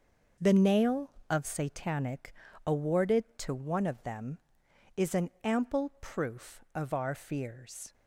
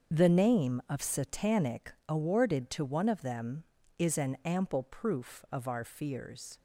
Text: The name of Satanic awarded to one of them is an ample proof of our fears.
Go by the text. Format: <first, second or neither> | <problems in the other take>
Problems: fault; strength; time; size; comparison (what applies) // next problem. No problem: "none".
second | starts louder than the rest; noticeable; until 1.5 s; 6 dB; also in the second // says "nail" for "name"; at 0.5 s // pauses between "Satanic" and "awarded"; slight; at 2.3 s; 0.32 s long; slight in the second